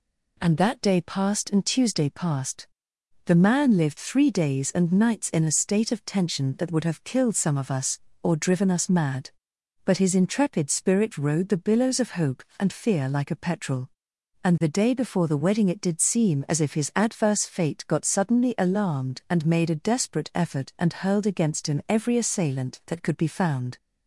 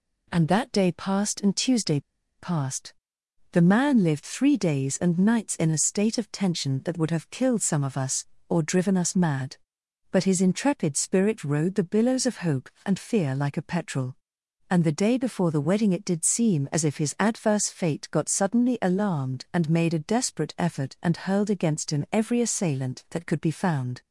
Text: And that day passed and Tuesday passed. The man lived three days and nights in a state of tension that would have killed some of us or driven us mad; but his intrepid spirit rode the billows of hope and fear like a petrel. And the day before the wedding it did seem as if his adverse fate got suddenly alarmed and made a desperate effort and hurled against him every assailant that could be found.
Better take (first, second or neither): first